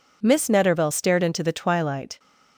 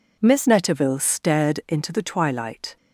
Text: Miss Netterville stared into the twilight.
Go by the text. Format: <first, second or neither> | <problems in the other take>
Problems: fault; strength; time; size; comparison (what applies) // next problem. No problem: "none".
first | changes voice at "Netterville"; from 0.4 s on; 2.3 s long